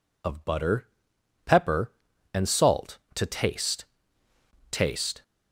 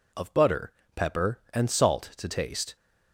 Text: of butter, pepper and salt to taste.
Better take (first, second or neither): second